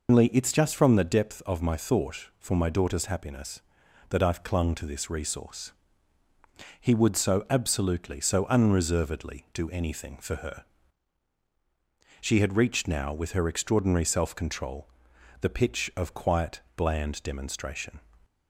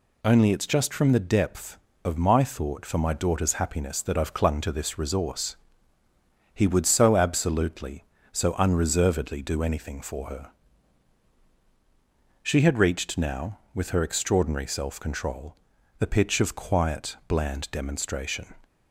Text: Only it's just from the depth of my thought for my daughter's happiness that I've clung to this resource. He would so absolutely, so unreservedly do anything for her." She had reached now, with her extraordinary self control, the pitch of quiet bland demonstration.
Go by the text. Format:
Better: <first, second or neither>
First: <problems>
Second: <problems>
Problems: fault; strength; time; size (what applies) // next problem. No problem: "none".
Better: second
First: loses the start of "Only"; at 0.0 s; 120 ms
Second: none